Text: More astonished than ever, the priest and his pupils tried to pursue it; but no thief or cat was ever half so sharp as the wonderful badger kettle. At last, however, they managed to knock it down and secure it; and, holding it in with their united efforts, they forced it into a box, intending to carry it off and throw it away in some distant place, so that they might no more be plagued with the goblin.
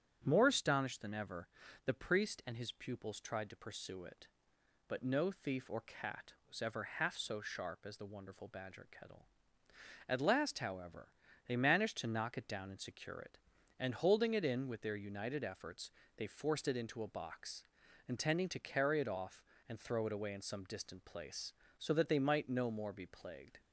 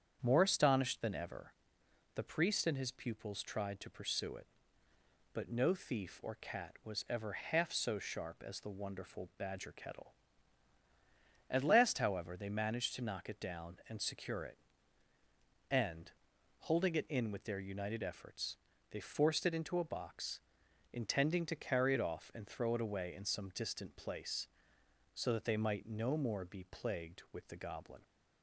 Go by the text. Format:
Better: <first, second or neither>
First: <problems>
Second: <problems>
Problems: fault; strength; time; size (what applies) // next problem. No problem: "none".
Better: second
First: starts louder than the rest; strong; until 1.2 s; 9 dB // stops before "with the goblin"; at 23.5 s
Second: starts louder than the rest; strong; until 1.2 s; 8 dB